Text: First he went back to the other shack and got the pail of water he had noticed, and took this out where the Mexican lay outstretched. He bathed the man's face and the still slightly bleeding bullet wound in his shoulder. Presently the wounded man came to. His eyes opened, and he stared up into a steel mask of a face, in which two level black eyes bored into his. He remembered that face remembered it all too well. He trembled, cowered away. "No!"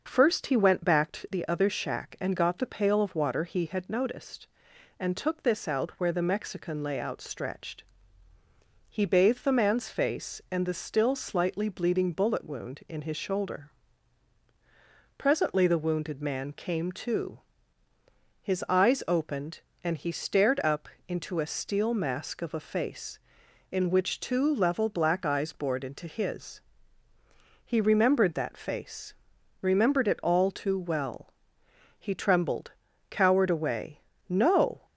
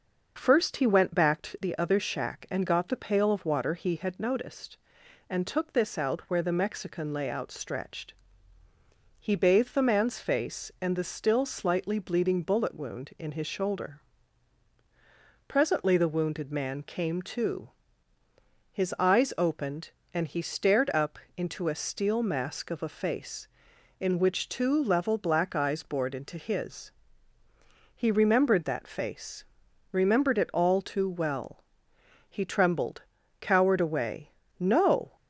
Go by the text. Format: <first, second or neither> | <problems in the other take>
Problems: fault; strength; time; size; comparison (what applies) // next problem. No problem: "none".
neither | starts louder than the rest; noticeable; the same in both // pauses between "up" and "into"; slight; the same in both // pauses between "face" and "remembered"; noticeable; the same in both